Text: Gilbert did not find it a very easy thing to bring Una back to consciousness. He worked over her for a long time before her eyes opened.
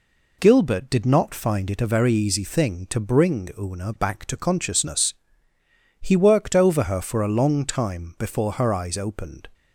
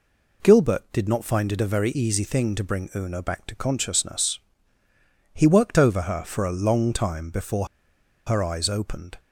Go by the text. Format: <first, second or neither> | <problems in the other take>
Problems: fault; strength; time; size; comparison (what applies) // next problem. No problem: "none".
first | pauses between "before" and "her"; noticeable; at 7.6 s; 0.60 s long